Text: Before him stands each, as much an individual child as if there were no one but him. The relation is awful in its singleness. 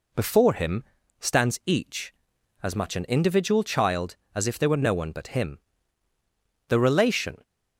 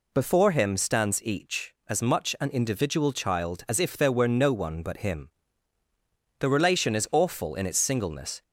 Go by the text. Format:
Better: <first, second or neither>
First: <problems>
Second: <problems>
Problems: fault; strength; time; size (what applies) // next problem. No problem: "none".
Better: second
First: pauses between "him" and "stands"; slight; at 0.8 s; 0.36 s long // stops before "is awful in its singleness"; at 7.4 s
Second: none